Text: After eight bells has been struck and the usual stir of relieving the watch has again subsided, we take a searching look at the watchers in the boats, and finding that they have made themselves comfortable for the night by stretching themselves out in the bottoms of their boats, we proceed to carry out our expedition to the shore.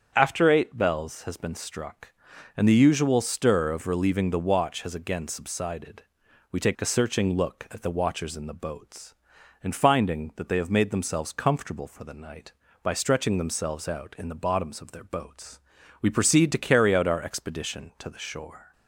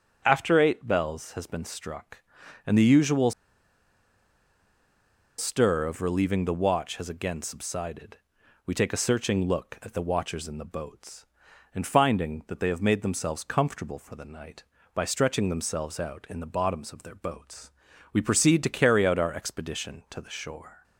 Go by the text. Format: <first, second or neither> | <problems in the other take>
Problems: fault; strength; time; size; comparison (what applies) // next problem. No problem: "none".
first | starts louder than the rest; strong; until 1.2 s; 7.5 dB; strong in the first // pauses between "usual" and "stir"; strong; at 3.3 s; 2.0 s long